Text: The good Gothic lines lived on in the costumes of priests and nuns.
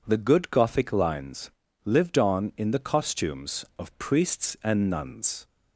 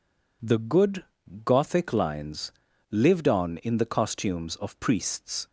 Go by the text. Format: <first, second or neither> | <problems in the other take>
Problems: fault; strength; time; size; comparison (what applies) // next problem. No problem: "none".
first | pauses between "good" and "Gothic"; at 1.0 s; 0.42 s long // pauses between "lines" and "lived"; at 2.5 s; 0.40 s long; slight in the first // stops before "and nuns"; at 5.4 s